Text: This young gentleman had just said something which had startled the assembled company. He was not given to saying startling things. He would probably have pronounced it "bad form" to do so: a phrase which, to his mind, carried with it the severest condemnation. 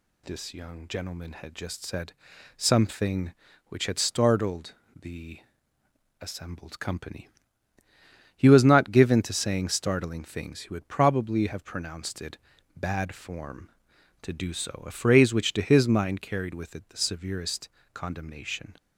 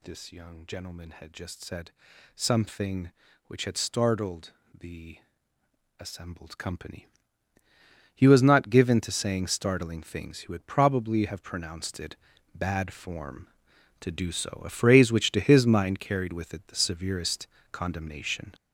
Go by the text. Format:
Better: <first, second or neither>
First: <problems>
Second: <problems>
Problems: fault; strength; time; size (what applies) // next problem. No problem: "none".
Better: first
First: pauses between "said" and "something"; at 2.1 s; 0.44 s long // pauses between "startled" and "the"; slight; at 4.7 s; 0.26 s long // pauses between "the" and "assembled"; noticeable; at 5.3 s; 0.82 s long // pauses between "it" and "bad"; at 12.3 s; 0.38 s long // pauses between "severest" and "condemnation"; slight; at 17.6 s; 0.24 s long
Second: gets louder; strong; throughout; 7 dB // pauses between "said" and "something"; at 1.9 s; 0.44 s long // pauses between "startled" and "the"; slight; at 4.5 s; 0.26 s long // pauses between "the" and "assembled"; noticeable; at 5.1 s; 0.82 s long // pauses between "it" and "bad"; at 12.1 s; 0.38 s long // pauses between "severest" and "condemnation"; slight; at 17.4 s; 0.24 s long